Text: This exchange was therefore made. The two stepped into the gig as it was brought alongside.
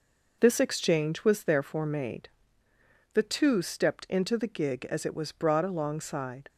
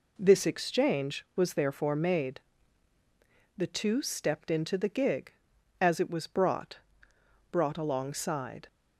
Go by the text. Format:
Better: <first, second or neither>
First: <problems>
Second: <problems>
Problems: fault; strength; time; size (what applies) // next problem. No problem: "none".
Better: first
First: none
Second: says "brought" twice; at 7.4 s